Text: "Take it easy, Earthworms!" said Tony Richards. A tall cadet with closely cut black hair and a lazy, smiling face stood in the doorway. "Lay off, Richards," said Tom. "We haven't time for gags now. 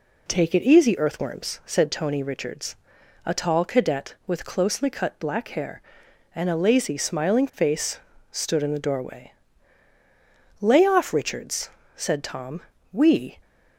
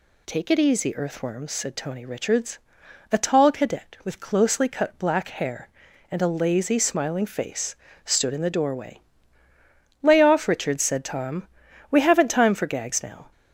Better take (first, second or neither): second